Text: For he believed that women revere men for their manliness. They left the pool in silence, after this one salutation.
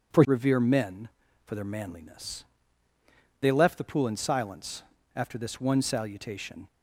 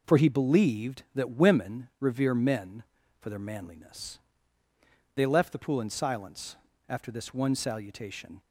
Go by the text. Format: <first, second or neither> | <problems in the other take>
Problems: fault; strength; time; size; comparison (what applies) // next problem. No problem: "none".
second | skips "he believed that women"; at 0.2 s